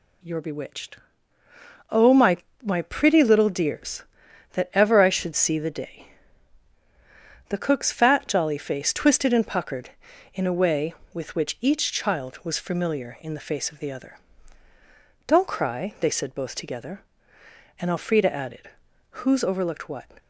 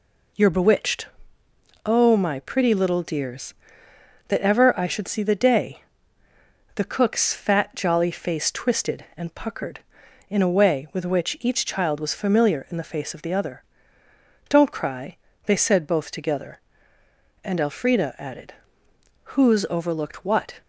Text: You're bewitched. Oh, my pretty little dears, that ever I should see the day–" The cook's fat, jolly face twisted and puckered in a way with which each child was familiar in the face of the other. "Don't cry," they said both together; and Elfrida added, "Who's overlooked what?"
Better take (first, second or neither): second